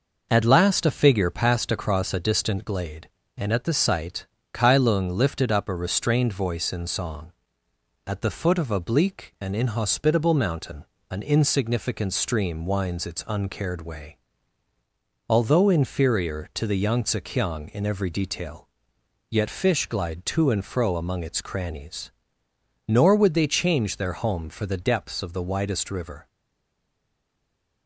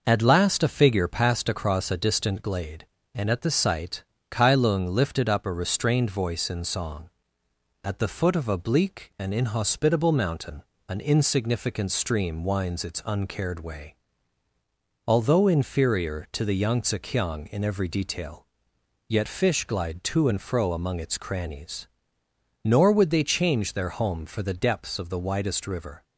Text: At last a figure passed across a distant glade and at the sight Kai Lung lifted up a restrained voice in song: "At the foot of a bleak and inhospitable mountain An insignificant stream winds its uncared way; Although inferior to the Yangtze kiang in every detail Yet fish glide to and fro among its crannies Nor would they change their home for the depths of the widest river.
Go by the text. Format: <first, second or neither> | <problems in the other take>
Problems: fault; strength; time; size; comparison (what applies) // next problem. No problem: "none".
second | pauses between "sight" and "Kai"; slight; at 4.2 s; 0.26 s long; slight in the second // pauses between "mountain" and "An"; slight; at 10.8 s; 0.26 s long; slight in the second // pauses between "detail" and "Yet"; noticeable; at 18.6 s; 0.64 s long; noticeable in the second // pauses between "crannies" and "Nor"; noticeable; at 22.1 s; 0.78 s long; noticeable in the second // stays silent after the last word; noticeable; from 26.2 s on; 1.6 s long